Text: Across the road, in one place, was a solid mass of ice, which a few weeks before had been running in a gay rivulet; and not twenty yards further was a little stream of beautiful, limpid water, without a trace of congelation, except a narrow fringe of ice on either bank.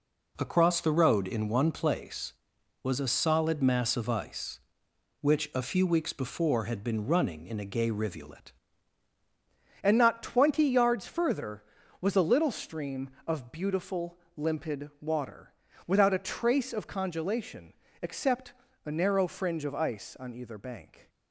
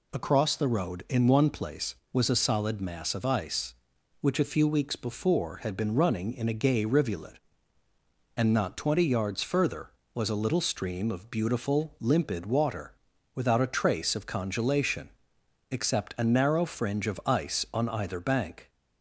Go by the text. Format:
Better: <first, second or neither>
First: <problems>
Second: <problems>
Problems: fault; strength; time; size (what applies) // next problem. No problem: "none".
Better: second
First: changes voice at "and"; from 9.8 s on; 11.2 s long // pauses between "except" and "a"; slight; at 18.5 s; 0.32 s long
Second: none